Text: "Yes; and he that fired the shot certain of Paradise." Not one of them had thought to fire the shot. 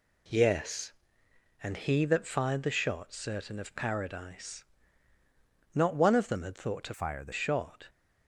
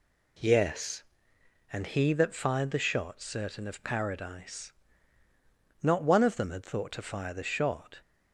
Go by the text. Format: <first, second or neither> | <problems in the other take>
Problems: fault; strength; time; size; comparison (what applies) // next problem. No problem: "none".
second | changes voice from "fire" to "the"; from 6.9 to 7.3 s; 0.4 s long